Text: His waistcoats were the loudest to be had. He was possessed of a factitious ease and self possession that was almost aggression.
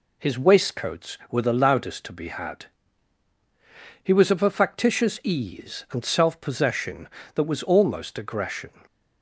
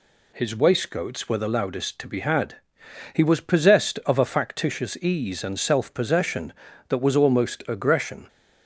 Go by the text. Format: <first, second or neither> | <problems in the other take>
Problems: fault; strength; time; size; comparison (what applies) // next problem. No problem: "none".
second | skips "possessed"; at 4.3 s